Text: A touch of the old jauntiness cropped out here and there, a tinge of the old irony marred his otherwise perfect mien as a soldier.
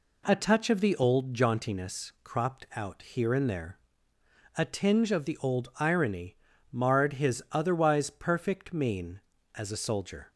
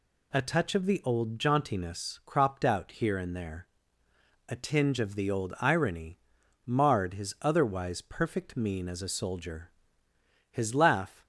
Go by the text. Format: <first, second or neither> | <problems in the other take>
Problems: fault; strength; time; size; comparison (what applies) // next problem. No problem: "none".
first | pauses between "irony" and "marred"; noticeable; at 6.1 s; 0.46 s long; slight in the first // goes on to say "His laugh"; noticeable; from 10.4 s on; 0.76 s long